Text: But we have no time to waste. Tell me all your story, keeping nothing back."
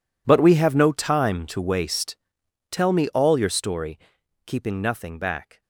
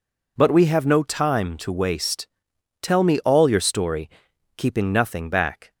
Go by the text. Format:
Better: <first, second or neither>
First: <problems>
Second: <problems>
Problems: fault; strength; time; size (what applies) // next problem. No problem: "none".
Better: second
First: gets quieter; strong; throughout; 18 dB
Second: none